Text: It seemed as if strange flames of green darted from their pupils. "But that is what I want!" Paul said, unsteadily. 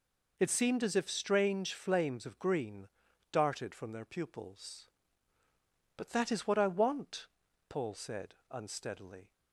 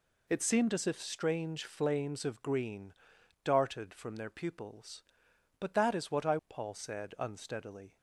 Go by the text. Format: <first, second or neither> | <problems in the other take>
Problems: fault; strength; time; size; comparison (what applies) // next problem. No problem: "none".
first | pauses between "green" and "darted"; noticeable; at 2.9 s; 0.52 s long; also in the first // skips "want"; at 6.4 s